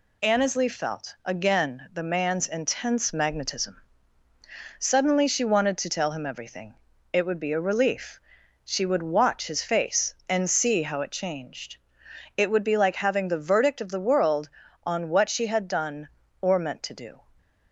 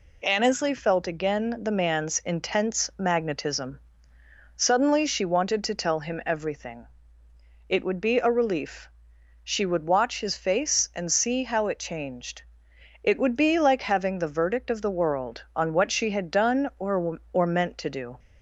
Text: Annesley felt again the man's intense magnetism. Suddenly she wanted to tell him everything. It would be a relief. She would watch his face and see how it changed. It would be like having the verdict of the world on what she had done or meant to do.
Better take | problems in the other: first | says "or" twice; at 17.3 s

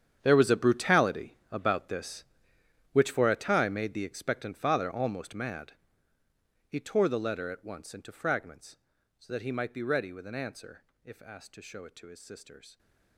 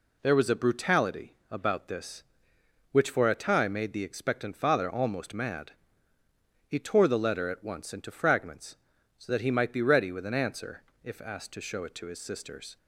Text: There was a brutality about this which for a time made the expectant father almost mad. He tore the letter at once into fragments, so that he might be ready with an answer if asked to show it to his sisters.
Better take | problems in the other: second | gets quieter; strong; throughout; 16 dB // pauses between "brutality" and "about"; slight; at 1.3 s; 0.16 s long; slight in the second // pauses between "answer" and "if"; slight; at 10.8 s; 0.22 s long; slight in the second

